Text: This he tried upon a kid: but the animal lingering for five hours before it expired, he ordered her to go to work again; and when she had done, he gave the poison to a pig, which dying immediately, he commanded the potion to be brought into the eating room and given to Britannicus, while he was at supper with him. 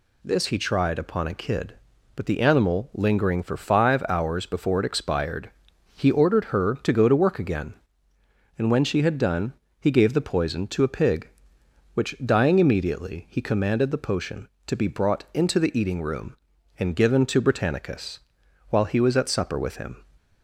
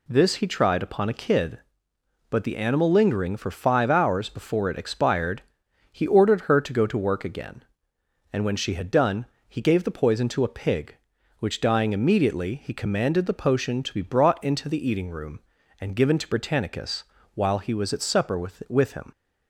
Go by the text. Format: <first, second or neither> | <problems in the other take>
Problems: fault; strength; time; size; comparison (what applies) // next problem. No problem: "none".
first | says "with" twice; at 18.6 s